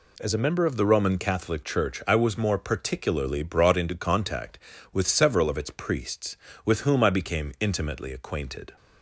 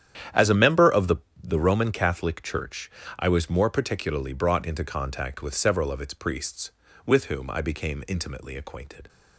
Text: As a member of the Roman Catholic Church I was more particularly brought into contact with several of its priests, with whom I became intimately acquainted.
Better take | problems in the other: first | starts louder than the rest; strong; until 1.6 s; 9.5 dB // says "the" twice; at 1.4 s // pauses between "Church" and "I"; slight; at 2.8 s; 0.30 s long

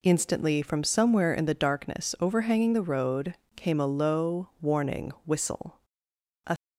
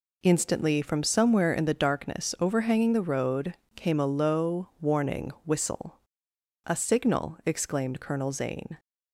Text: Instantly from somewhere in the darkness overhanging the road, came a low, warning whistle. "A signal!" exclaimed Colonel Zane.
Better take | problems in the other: second | stops before "signal exclaimed Colonel Zane"; at 6.5 s

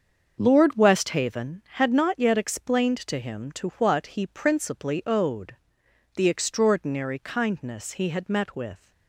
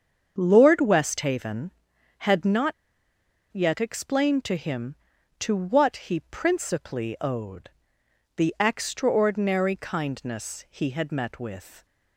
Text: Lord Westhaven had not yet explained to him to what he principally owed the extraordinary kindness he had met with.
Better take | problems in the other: first | starts louder than the rest; until 1.3 s; 7 dB; also in the first // pauses between "not" and "yet"; noticeable; at 2.7 s; 0.79 s long // pauses between "owed" and "the"; noticeable; at 7.6 s; 0.68 s long; noticeable in the first

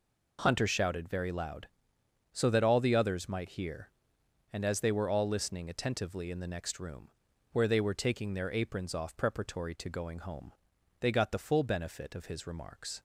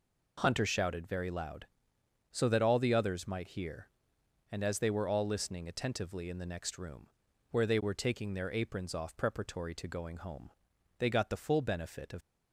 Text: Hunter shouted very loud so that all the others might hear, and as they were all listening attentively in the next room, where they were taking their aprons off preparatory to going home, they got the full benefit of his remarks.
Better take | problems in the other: first | stops before "his remarks"; at 12.2 s

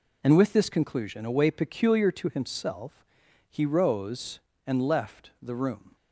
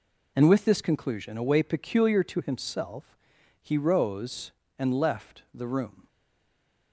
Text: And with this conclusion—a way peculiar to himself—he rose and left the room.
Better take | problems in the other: first | stays silent after the last word; slight; from 6.0 s on; 0.9 s long

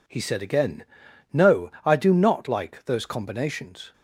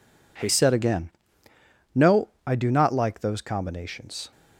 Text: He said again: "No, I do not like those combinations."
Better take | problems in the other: first | changes voice at "said"; from 0.4 s on; 3.9 s long

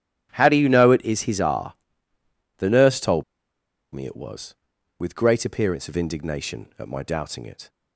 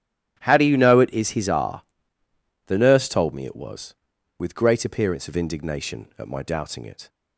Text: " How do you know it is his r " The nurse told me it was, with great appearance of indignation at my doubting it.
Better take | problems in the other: second | starts louder than the rest; strong; until 1.3 s; 10 dB; strong in the second // pauses between "told" and "me"; noticeable; at 3.2 s; 0.71 s long

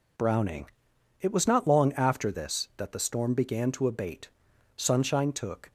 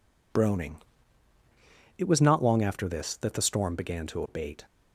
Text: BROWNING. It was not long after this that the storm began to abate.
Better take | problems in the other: second | goes on to say "Sunshine took"; noticeable; from 4.7 s on; 0.94 s long

